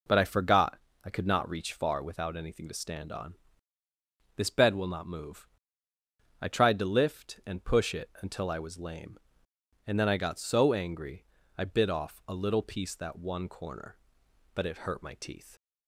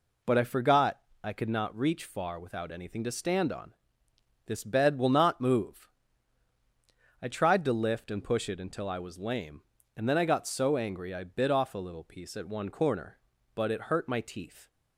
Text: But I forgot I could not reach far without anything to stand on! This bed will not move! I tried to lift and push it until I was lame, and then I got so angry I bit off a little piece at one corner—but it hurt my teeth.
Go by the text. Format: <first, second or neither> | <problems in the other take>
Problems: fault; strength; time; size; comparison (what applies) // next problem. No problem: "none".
second | pauses between "forgot" and "I"; slight; at 0.7 s; 0.28 s long; slight in the second // pauses between "angry" and "I"; slight; at 11.2 s; 0.32 s long // says "that" for "at"; at 12.9 s